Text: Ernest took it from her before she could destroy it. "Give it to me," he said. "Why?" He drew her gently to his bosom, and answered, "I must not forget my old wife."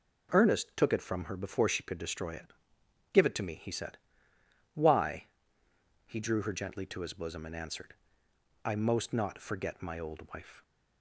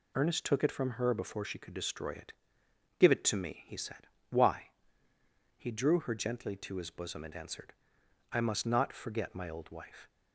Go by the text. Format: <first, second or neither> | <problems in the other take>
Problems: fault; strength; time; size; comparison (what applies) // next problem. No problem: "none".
second | says "most" for "must"; at 8.7 s